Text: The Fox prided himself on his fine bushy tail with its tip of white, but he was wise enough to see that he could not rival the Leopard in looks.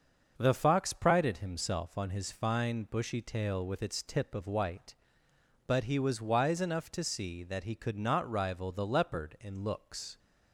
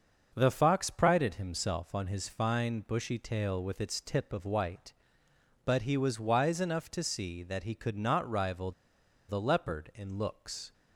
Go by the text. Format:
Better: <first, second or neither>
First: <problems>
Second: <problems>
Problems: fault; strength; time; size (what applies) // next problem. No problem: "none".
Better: first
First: starts louder than the rest; until 1.3 s; 6.5 dB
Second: starts louder than the rest; until 1.3 s; 6.5 dB // pauses between "rival" and "the"; noticeable; at 8.7 s; 0.56 s long